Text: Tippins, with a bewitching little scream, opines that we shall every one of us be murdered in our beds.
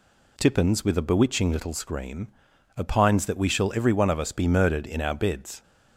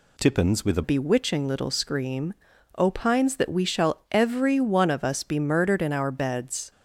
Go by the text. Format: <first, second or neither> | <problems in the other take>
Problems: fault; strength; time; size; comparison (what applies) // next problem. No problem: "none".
first | changes voice at "bewitching"; from 0.8 s on; 5.9 s long